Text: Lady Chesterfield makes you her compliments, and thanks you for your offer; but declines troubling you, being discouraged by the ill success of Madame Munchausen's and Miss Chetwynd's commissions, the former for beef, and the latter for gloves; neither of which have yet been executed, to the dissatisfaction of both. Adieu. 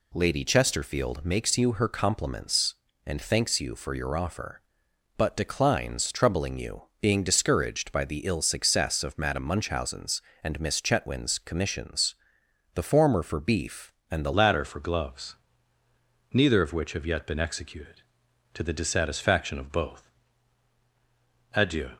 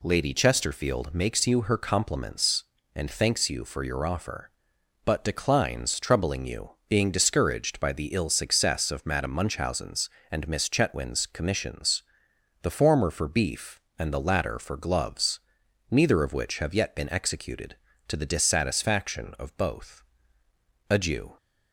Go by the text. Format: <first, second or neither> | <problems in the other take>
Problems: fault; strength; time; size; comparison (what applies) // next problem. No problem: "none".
second | changes voice at "latter"; from 14.3 s on; 7.5 s long